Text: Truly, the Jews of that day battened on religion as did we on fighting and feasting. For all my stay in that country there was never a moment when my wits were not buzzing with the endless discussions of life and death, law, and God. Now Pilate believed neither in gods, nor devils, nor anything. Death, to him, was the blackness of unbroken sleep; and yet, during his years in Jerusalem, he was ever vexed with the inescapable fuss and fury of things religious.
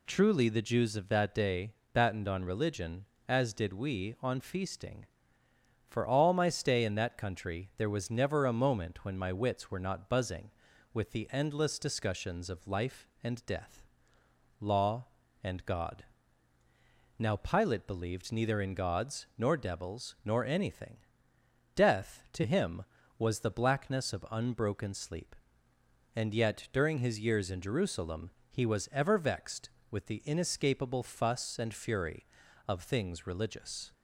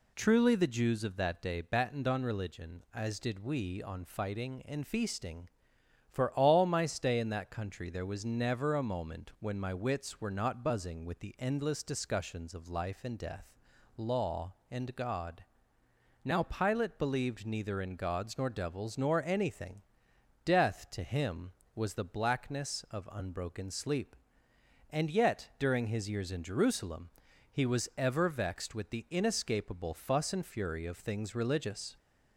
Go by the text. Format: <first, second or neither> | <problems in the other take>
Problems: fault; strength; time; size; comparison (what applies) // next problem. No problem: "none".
second | pauses between "day" and "battened"; slight; at 1.7 s; 0.20 s long // skips "fighting and"; at 4.3 s